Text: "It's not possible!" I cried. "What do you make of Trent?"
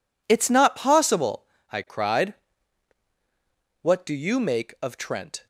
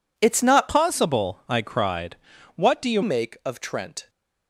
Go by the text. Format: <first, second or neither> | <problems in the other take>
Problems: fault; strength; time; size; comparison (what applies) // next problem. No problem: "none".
first | changes voice from "possible" to "you"; from 0.6 to 3.0 s; 2.4 s long